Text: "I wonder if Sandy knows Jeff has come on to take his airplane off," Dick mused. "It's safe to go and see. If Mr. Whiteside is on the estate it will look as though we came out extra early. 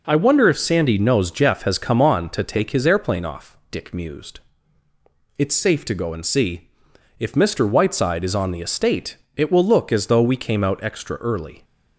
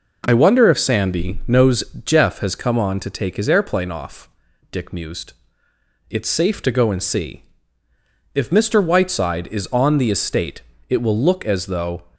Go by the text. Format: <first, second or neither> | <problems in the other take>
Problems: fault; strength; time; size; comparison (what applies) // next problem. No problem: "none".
first | pauses between "knows" and "Jeff"; slight; at 1.8 s; 0.22 s long // pauses between "estate" and "it"; slight; at 10.6 s; 0.26 s long; slight in the first // stops before "we came out extra early"; at 12.1 s